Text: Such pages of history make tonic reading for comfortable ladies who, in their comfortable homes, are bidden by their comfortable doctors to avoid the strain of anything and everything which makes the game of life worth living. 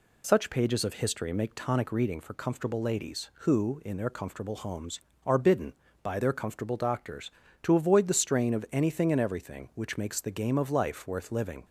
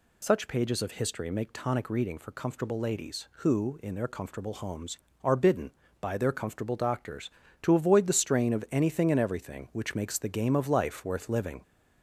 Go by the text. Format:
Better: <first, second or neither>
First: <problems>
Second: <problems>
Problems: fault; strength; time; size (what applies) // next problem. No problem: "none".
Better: first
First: none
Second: gets louder; slight; throughout; 2.5 dB